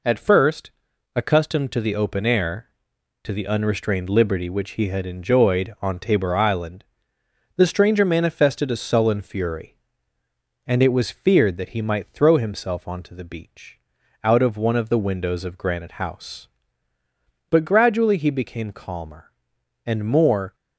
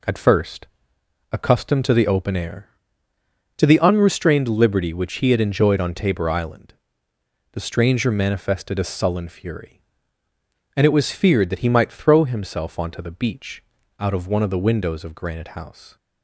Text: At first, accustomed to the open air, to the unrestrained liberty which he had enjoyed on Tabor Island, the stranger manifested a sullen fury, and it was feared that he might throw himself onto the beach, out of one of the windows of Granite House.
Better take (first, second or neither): second